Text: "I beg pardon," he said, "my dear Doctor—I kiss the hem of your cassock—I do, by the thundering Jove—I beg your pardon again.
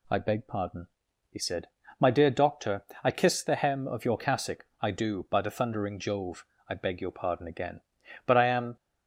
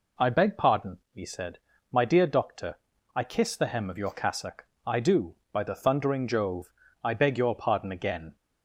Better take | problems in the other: second | goes on to say "But I am"; from 8.2 s on; 0.52 s long

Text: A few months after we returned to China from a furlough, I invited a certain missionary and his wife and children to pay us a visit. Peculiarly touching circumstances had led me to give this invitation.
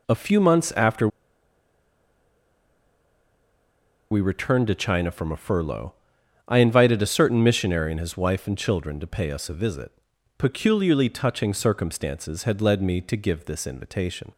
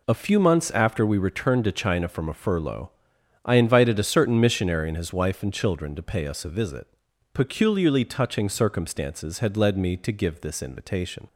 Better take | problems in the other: second | pauses between "after" and "we"; strong; at 1.0 s; 3.0 s long

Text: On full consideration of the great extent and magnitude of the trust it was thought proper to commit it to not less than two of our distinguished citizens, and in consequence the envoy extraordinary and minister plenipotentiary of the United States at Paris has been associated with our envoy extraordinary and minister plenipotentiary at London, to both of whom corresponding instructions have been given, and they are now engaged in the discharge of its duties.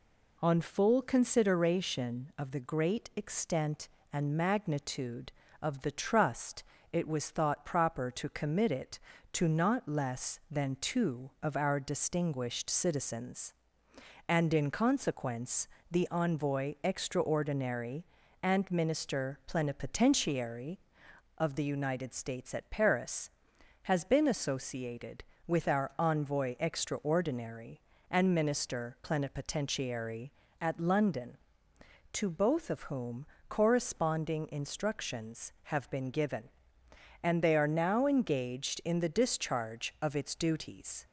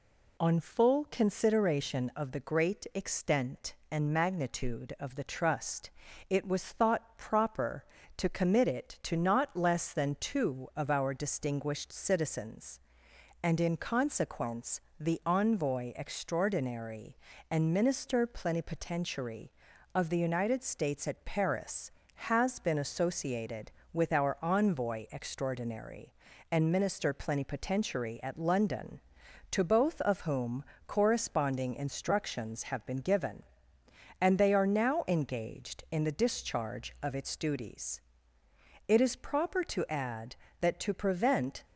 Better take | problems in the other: first | pauses between "trust" and "it"; slight; at 5.9 s; 0.36 s long; slight in the first // pauses between "consequence" and "the"; slight; at 14.7 s; 0.20 s long; slight in the first // pauses between "whom" and "corresponding"; slight; at 30.6 s; 0.22 s long; slight in the first // goes on to say "It is proper to add that to prevent"; strong; from 38.8 s on; 2.7 s long

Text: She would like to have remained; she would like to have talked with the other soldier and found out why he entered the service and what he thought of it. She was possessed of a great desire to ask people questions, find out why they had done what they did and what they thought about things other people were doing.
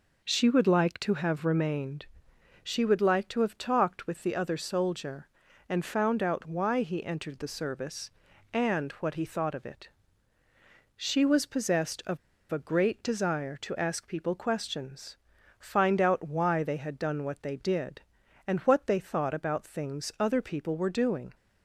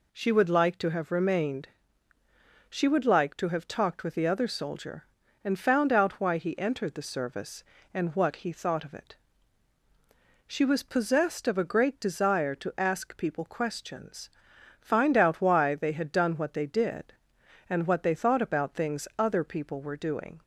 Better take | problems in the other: second | pauses between "of" and "a"; slight; at 12.1 s; 0.34 s long

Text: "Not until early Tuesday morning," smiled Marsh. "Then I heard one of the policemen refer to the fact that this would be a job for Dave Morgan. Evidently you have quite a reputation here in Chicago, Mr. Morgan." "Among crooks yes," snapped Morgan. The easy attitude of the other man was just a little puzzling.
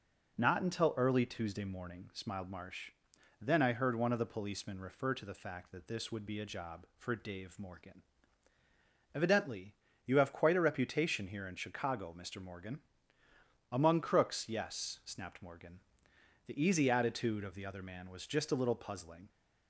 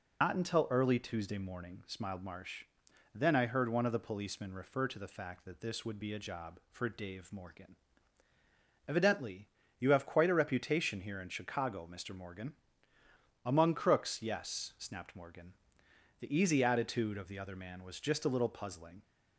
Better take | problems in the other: first | loses the start of "Not"; at 0.2 s; 110 ms // pauses between "Evidently" and "you"; slight; at 9.4 s; 0.30 s long; slight in the first

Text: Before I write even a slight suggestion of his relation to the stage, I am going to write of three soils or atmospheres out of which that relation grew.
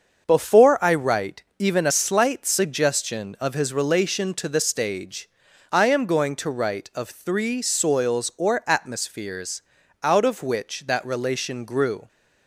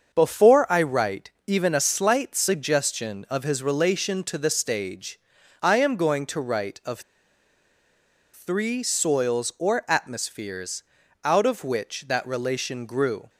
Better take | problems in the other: first | starts louder than the rest; until 1.1 s; 6.5 dB; also in the first // pauses between "write" and "even"; slight; at 1.3 s; 0.16 s long; slight in the first // pauses between "of" and "three"; strong; at 7.0 s; 1.3 s long // pauses between "atmospheres" and "out"; at 10.8 s; 0.42 s long; also in the first

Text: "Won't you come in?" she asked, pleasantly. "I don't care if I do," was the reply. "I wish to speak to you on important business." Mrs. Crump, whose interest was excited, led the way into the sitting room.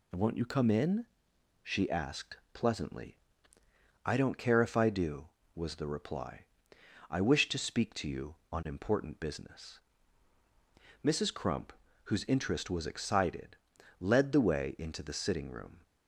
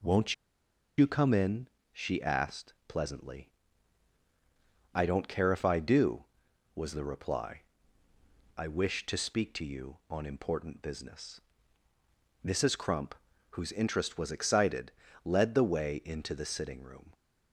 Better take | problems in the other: first | pauses between "Won't" and "you"; noticeable; at 0.3 s; 0.64 s long

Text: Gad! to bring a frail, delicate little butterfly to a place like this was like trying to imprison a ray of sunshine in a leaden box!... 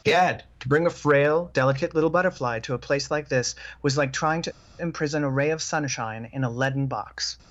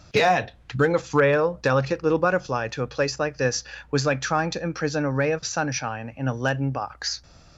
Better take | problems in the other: second | pauses between "to" and "imprison"; slight; at 4.5 s; 0.30 s long

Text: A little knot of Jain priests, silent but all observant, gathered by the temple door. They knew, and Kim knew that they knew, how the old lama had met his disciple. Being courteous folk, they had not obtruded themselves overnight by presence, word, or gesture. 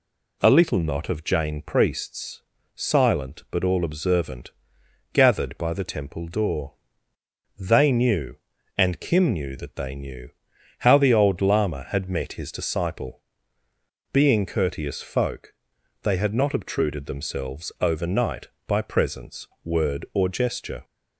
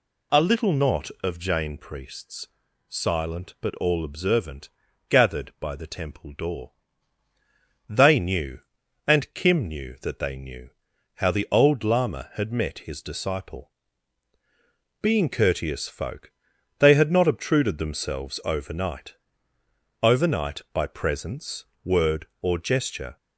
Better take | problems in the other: first | says "overnight" twice; at 20.0 s

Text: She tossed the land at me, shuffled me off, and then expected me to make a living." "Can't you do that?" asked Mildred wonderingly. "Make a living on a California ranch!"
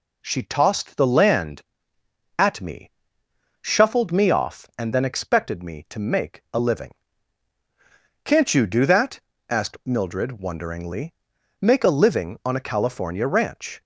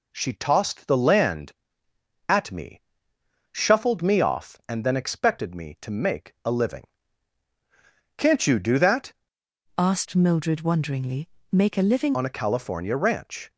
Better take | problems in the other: first | changes voice from "asked" to "living"; from 9.7 to 12.1 s; 2.4 s long

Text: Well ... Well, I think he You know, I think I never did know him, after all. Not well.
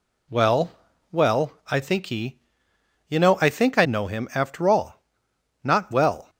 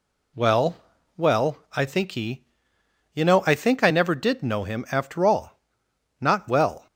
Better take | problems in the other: second | pauses between "he" and "You"; noticeable; at 2.3 s; 0.68 s long; noticeable in the second // skips "never did"; at 3.8 s

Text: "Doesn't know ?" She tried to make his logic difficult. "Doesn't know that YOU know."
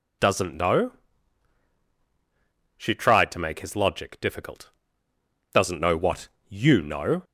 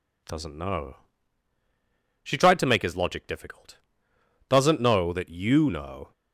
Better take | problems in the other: second | says "what" for "that"; at 5.9 s

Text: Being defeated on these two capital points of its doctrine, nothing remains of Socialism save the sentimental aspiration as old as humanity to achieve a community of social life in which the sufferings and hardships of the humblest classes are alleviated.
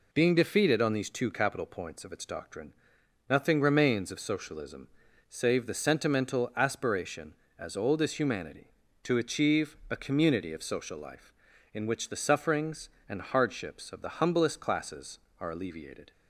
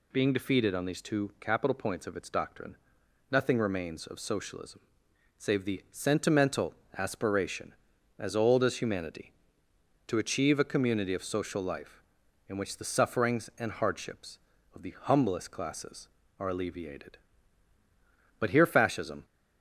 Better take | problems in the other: first | pauses between "Socialism" and "save"; noticeable; at 4.8 s; 0.56 s long; also in the first // pauses between "sentimental" and "aspiration"; slight; at 6.7 s; 0.24 s long // goes on to say "But here Fascism"; noticeable; from 18.3 s on; 0.86 s long

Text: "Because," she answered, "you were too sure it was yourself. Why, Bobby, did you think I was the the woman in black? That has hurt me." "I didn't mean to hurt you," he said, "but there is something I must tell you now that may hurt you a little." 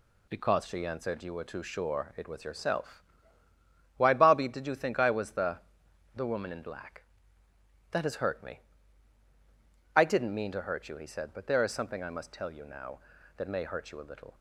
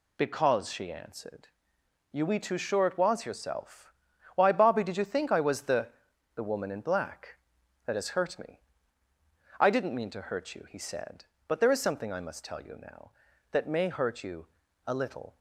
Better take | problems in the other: first | says "we" for "were"; at 2.2 s // pauses between "the" and "the"; noticeable; at 5.8 s; 0.46 s long; noticeable in the first // pauses between "you" and "a"; at 14.4 s; 0.38 s long

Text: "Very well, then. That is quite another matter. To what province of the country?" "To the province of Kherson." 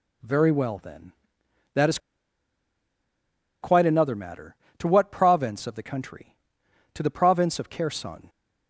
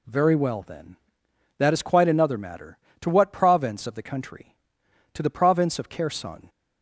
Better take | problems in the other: second | pauses between "is" and "quite"; strong; at 1.9 s; 1.6 s long

